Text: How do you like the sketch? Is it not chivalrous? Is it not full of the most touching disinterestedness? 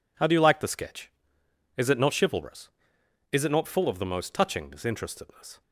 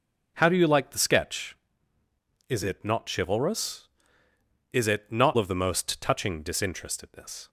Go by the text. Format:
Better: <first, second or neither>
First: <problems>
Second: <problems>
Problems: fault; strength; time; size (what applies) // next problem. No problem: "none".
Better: first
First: none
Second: skips "full"; at 5.3 s